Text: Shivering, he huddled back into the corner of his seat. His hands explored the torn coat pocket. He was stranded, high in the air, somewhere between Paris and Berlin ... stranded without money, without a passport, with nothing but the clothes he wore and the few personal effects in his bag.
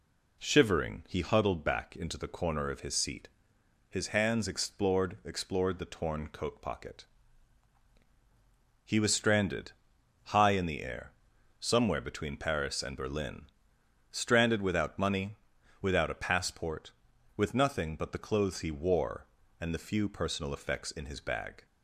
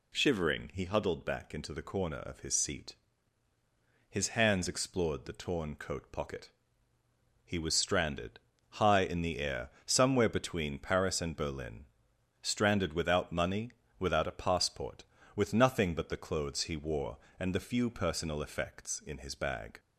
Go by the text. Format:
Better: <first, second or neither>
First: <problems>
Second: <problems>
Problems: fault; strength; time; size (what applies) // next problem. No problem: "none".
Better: second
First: says "explored" twice; at 5.2 s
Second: none